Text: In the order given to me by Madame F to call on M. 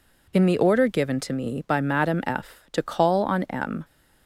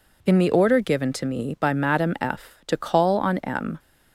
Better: neither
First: none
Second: none

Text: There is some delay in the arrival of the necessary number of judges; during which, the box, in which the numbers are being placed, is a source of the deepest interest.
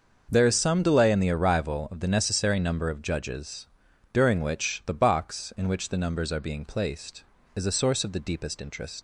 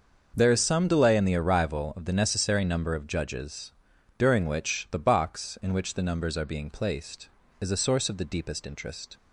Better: second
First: starts louder than the rest; until 1.3 s; 6.5 dB // leaves "interest" unfinished; at 8.9 s; 100 ms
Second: starts louder than the rest; until 1.3 s; 6.5 dB

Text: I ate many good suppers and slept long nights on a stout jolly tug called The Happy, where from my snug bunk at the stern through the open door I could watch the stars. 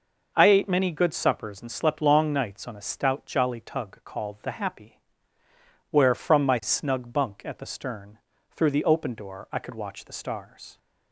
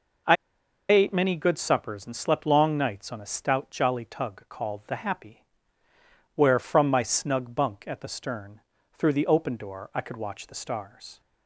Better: first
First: pauses between "stern" and "through"; slight; at 8.1 s; 0.34 s long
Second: pauses between "I" and "ate"; noticeable; at 0.3 s; 0.56 s long // pauses between "stern" and "through"; slight; at 8.5 s; 0.34 s long

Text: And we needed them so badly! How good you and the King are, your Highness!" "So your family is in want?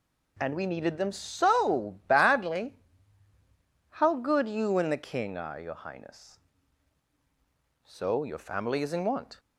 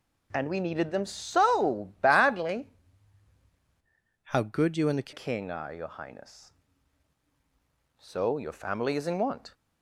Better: first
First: none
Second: changes voice from "How" to "the"; from 4.2 to 5.1 s; 0.9 s long

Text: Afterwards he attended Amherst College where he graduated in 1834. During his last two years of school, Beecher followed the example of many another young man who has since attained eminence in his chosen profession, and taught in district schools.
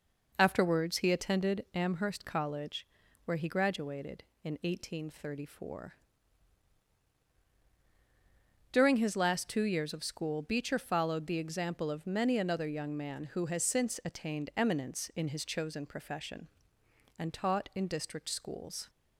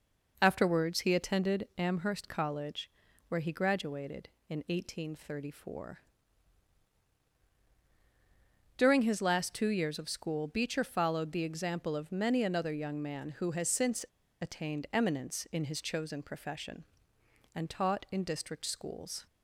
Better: first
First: pauses between "College" and "where"; at 2.8 s; 0.40 s long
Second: pauses between "College" and "where"; at 2.8 s; 0.40 s long // pauses between "since" and "attained"; at 14.0 s; 0.37 s long

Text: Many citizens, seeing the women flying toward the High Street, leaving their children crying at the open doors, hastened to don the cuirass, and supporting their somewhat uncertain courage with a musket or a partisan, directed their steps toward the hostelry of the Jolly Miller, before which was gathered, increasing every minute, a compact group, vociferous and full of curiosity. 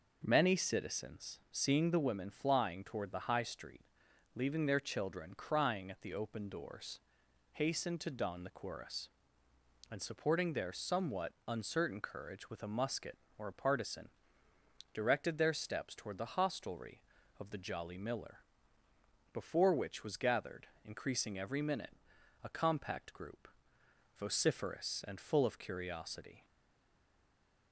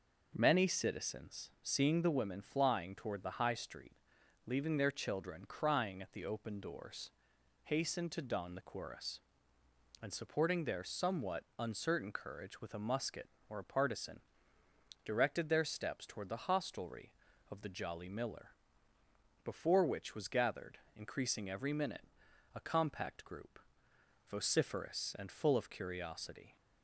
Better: second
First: pauses between "somewhat" and "uncertain"; slight; at 11.3 s; 0.16 s long // stays silent after the last word; noticeable; from 26.4 s on; 1.3 s long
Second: pauses between "somewhat" and "uncertain"; slight; at 11.4 s; 0.16 s long

